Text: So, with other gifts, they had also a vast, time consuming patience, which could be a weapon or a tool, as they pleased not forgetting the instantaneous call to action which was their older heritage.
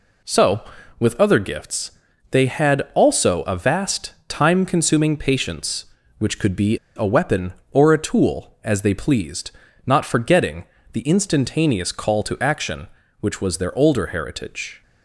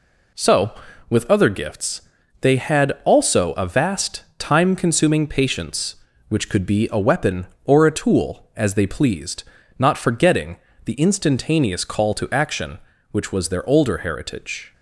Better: second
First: pauses between "be" and "a"; slight; at 6.7 s; 0.19 s long // pauses between "pleased" and "not"; slight; at 9.5 s; 0.34 s long // pauses between "forgetting" and "the"; slight; at 10.6 s; 0.26 s long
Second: pauses between "pleased" and "not"; slight; at 9.4 s; 0.34 s long // pauses between "forgetting" and "the"; slight; at 10.5 s; 0.26 s long

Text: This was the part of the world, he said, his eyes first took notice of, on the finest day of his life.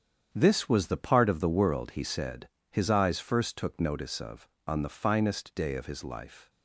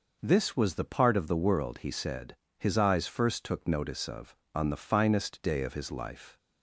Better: second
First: gets quieter; strong; throughout; 9.5 dB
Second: none

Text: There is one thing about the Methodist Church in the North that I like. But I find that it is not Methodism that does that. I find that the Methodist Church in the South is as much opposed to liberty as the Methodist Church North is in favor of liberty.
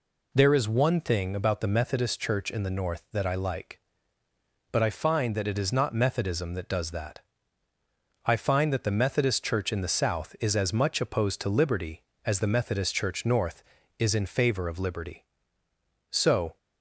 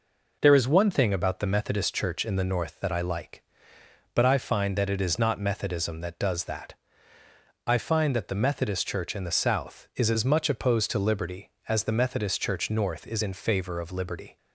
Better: second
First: goes on to say "So"; slight; from 16.1 s on; 0.46 s long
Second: none

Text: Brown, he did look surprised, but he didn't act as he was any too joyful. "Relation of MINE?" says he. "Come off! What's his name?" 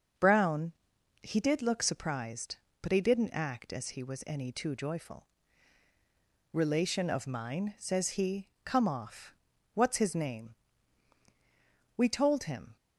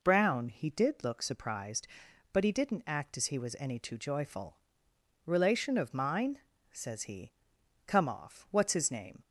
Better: second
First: starts louder than the rest; until 1.6 s; 6.5 dB // goes on to say "We told him"; noticeable; from 11.9 s on; 0.78 s long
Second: none

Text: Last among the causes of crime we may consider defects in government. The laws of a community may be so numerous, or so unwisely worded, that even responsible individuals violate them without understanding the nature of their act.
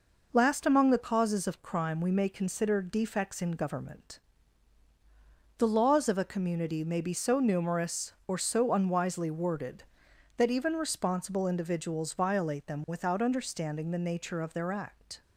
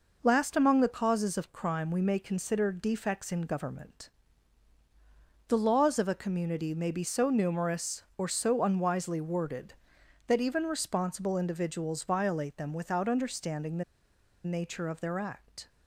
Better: first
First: none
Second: pauses between "the" and "nature"; noticeable; at 13.8 s; 0.62 s long

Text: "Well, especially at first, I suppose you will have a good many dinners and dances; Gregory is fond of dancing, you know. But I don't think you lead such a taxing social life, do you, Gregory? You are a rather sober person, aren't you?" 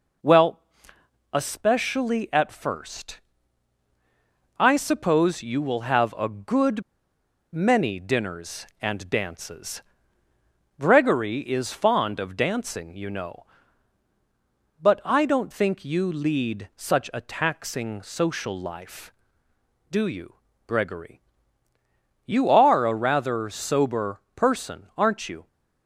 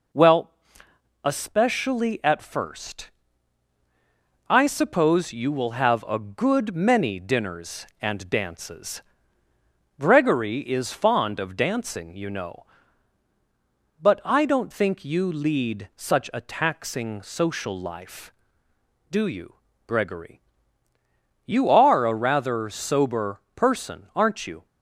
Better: second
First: pauses between "good" and "many"; noticeable; at 6.8 s; 0.72 s long // pauses between "sober" and "person"; slight; at 24.2 s; 0.16 s long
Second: pauses between "sober" and "person"; slight; at 23.4 s; 0.16 s long

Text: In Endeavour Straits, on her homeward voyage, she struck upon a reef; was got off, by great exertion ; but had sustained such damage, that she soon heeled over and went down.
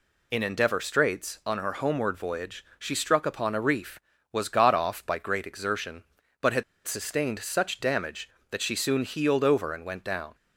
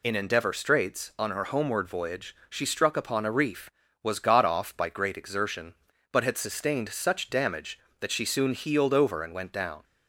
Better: second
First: pauses between "had" and "sustained"; slight; at 6.6 s; 0.23 s long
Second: none

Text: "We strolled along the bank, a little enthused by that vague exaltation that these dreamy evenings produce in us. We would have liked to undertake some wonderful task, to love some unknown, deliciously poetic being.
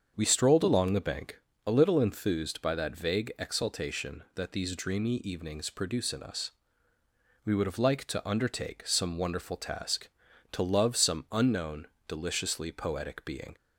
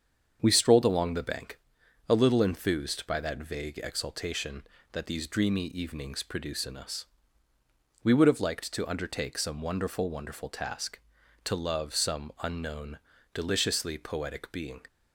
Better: first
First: starts louder than the rest; until 1.1 s; 7 dB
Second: starts louder than the rest; strong; until 1.4 s; 7.5 dB // says "wonderful" twice; at 10.0 s

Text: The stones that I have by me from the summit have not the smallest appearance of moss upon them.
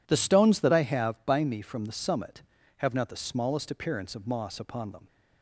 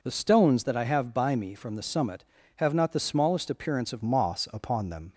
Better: first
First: none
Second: changes voice at "moss"; from 4.0 s on; 1.1 s long

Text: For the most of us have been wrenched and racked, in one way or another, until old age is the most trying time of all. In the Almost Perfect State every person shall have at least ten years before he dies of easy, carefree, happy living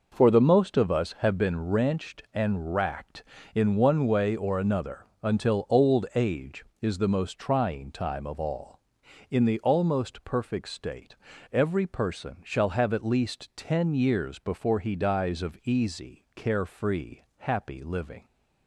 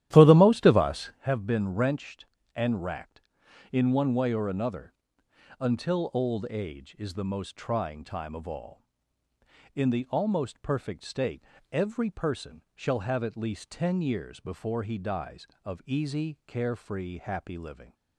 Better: first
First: pauses between "State" and "every"; slight; at 11.1 s; 0.36 s long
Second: starts louder than the rest; strong; until 1.2 s; 12.5 dB // pauses between "State" and "every"; slight; at 11.4 s; 0.30 s long

